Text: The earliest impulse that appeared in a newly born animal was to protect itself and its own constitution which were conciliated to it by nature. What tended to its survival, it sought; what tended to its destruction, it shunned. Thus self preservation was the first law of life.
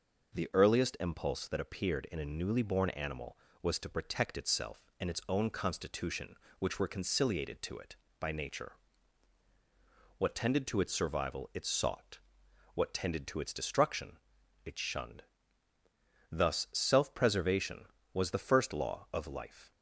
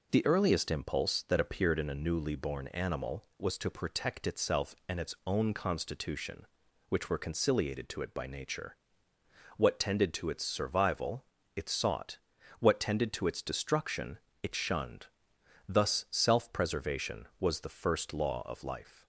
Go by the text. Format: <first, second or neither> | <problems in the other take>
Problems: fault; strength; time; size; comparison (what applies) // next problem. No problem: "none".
neither | none